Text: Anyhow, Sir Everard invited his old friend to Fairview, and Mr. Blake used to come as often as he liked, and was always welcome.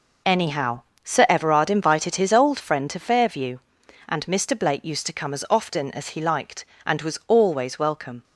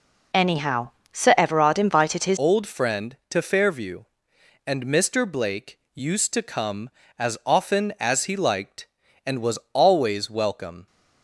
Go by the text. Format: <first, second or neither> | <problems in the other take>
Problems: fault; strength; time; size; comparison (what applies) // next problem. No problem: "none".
first | changes voice at "old"; from 2.3 s on; 8.5 s long // pauses between "Blake" and "used"; slight; at 5.7 s; 0.18 s long